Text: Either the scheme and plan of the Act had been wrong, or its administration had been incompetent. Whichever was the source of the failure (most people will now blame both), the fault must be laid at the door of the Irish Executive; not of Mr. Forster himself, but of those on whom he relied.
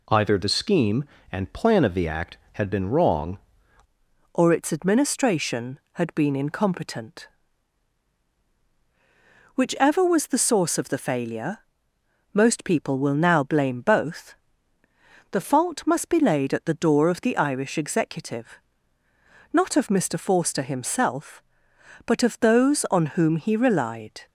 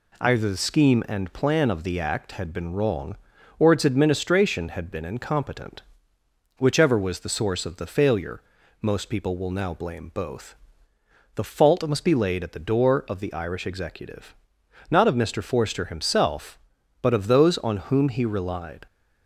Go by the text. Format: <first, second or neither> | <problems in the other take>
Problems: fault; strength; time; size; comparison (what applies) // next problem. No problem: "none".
second | changes voice at "or"; from 4.3 s on; 19.9 s long